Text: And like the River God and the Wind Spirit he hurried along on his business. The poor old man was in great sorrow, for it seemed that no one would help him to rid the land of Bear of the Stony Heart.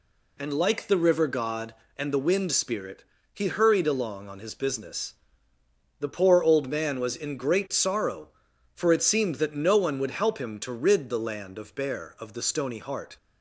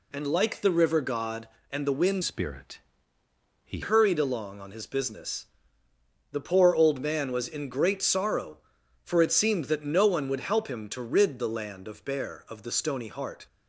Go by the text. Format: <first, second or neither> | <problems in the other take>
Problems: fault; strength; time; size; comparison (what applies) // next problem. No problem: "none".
first | changes voice from "Spirit" to "he"; from 2.2 to 3.7 s; 1.5 s long // pauses between "Spirit" and "he"; noticeable; at 2.7 s; 0.84 s long; slight in the first